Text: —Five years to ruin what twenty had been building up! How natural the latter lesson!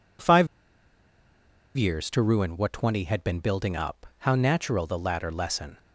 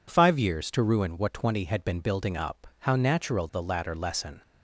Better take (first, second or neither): second